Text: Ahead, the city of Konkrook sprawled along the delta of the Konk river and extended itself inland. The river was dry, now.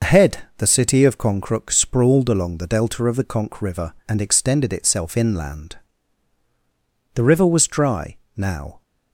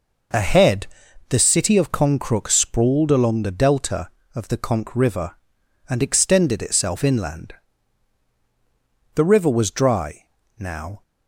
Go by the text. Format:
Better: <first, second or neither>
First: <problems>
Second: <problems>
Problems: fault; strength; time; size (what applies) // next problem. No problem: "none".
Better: second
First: loses the start of "Ahead"; at 0.0 s; 75 ms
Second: none